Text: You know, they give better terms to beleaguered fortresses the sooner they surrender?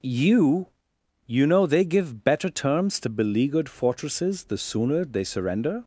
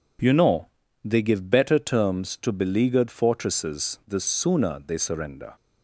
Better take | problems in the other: second | says "You" twice; at 1.2 s

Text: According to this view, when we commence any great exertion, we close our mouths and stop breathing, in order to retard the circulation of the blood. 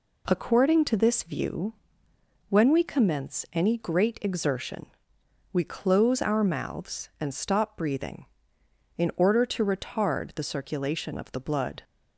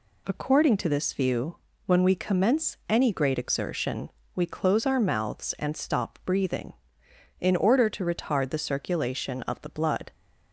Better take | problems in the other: neither | none

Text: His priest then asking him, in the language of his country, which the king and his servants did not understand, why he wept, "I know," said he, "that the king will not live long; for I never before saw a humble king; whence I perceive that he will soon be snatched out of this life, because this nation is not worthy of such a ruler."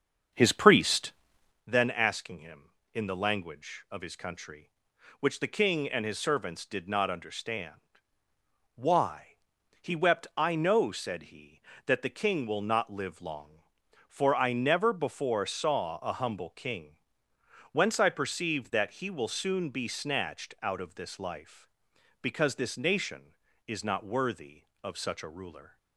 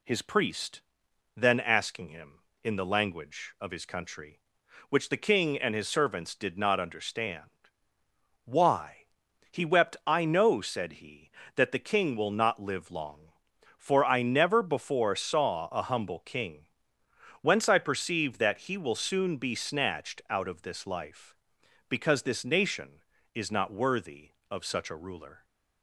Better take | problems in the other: second | starts louder than the rest; until 1.7 s; 7 dB // pauses between "priest" and "then"; noticeable; at 1.1 s; 0.54 s long; noticeable in the second // pauses between "why" and "he"; at 9.3 s; 0.44 s long; also in the second

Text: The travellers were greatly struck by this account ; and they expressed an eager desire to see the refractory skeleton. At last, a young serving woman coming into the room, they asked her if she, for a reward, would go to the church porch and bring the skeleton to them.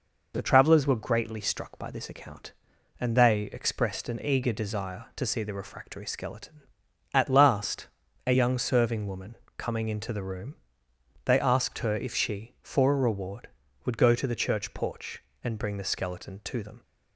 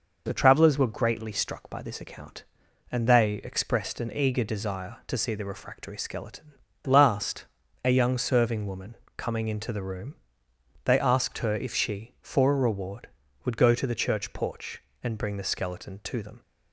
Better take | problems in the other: first | skips "At"; at 6.7 s // pauses between "woman" and "coming"; slight; at 8.9 s; 0.20 s long; slight in the first

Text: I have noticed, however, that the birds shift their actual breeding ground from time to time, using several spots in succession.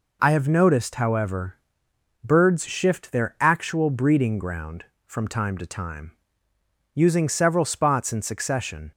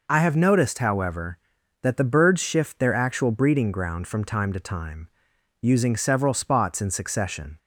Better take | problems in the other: second | skips "that the"; at 1.8 s

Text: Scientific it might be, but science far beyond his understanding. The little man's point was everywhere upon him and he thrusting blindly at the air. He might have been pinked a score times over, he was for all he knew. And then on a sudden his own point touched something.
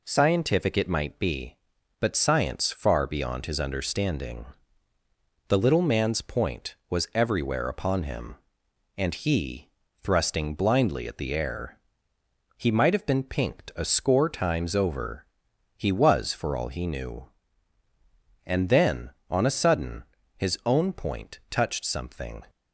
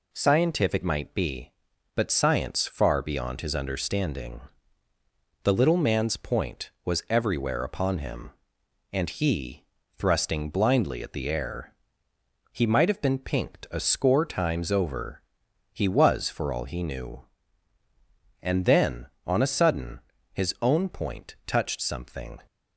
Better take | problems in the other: first | skips "it"; at 0.8 s // pauses between "he" and "thrusting"; slight; at 9.6 s; 0.34 s long; slight in the first // pauses between "sudden" and "his"; slight; at 19.9 s; 0.32 s long; slight in the first

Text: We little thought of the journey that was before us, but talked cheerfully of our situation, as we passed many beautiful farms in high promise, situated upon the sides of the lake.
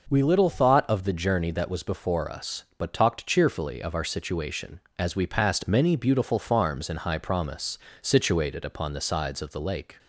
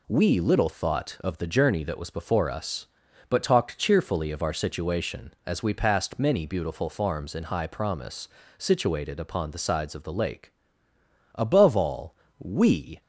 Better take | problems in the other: first | goes on to say "Above all we"; from 11.3 s on; 1.6 s long

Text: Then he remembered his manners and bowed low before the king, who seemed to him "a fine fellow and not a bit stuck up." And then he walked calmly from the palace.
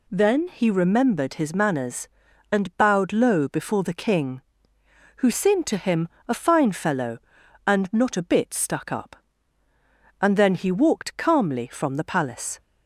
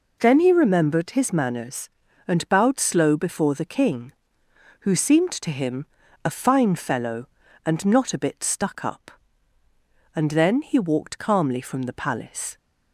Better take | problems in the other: first | says "slow" for "low"; at 2.7 s // pauses between "him" and "a"; at 5.8 s; 0.38 s long; slight in the first

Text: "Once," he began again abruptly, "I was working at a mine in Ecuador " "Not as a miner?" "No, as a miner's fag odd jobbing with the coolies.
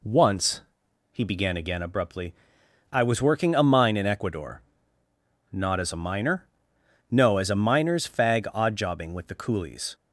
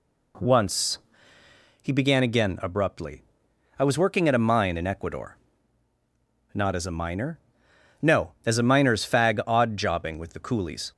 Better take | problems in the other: second | skips "at"; at 3.5 s

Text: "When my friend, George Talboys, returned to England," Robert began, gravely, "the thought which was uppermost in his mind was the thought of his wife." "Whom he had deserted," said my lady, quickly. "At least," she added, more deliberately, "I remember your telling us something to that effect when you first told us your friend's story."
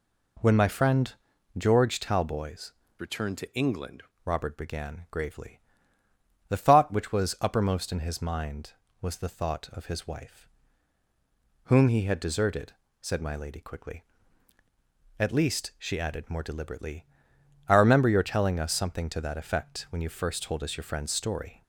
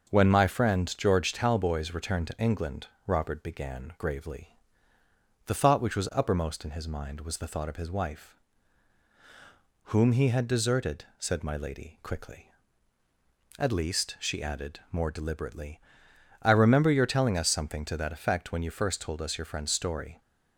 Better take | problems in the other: second | changes voice from "returned" to "England"; from 3.0 to 4.0 s; 1.0 s long

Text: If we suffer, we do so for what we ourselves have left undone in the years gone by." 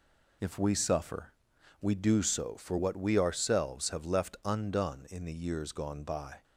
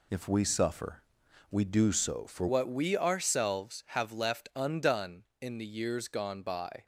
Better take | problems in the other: first | changes voice at "what"; from 2.4 s on; 4.4 s long

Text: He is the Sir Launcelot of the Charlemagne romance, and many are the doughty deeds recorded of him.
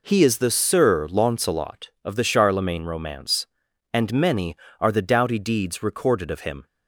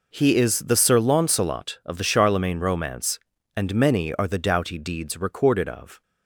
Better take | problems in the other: first | stops before "him"; at 6.0 s

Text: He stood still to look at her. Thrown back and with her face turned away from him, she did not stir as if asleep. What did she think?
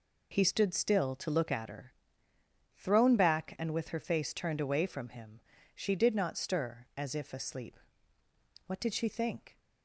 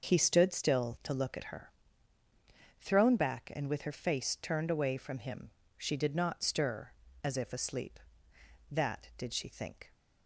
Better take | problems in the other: first | says "That" for "What"; at 8.6 s

